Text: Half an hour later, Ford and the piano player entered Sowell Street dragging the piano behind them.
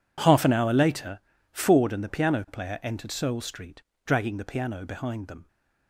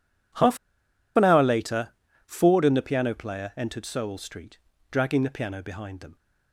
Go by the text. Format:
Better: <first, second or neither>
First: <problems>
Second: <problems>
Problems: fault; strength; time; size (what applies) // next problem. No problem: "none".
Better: first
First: pauses between "Street" and "dragging"; slight; at 3.8 s; 0.24 s long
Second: pauses between "Half" and "an"; noticeable; at 0.5 s; 0.58 s long // pauses between "Street" and "dragging"; slight; at 4.5 s; 0.34 s long